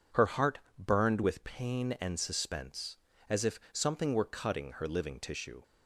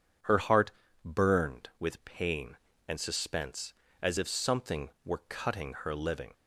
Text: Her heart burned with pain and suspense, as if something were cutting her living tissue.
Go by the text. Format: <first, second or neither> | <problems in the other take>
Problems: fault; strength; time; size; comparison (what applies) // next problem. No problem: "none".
first | pauses between "heart" and "burned"; slight; at 0.7 s; 0.34 s long; slight in the first // stops before "tissue"; at 6.3 s